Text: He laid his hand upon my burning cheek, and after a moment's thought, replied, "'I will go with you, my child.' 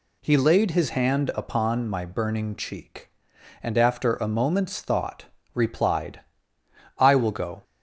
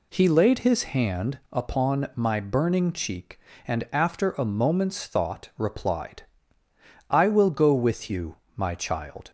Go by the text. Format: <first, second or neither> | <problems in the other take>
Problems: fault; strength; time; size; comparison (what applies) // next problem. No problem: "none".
second | stops before "with you my child"; at 7.6 s